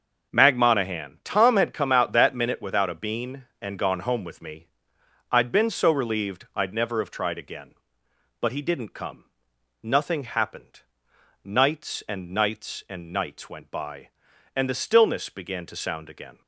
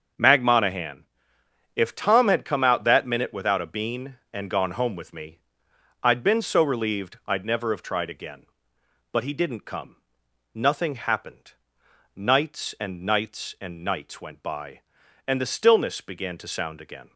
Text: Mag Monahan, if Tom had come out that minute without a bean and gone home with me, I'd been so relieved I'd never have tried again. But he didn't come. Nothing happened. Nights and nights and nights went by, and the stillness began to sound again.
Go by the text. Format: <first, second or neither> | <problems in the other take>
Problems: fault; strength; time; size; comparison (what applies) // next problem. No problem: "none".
second | starts louder than the rest; until 1.3 s; 6 dB; also in the second // skips "if"; at 1.2 s